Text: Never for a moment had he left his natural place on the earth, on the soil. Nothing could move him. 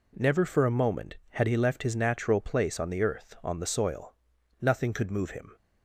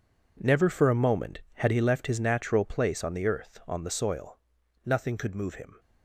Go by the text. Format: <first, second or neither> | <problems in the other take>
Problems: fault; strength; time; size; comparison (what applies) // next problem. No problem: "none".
first | gets quieter; strong; throughout; 13 dB